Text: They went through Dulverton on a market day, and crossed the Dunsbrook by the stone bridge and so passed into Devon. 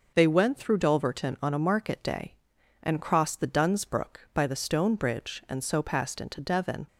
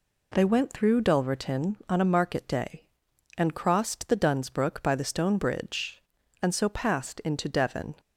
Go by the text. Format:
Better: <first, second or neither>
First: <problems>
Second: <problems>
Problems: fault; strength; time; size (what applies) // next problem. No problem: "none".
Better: neither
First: none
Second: none